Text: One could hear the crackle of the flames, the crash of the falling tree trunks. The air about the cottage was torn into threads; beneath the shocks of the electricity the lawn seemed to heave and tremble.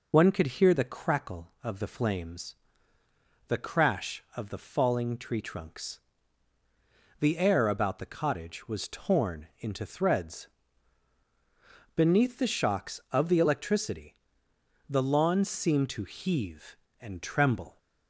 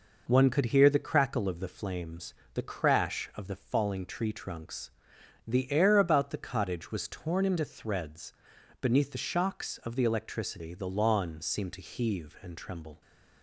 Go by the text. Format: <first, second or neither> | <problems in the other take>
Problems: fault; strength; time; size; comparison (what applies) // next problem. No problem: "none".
second | loses the start of "One"; at 0.1 s; 35 ms // pauses between "electricity" and "the"; noticeable; at 14.1 s; 0.74 s long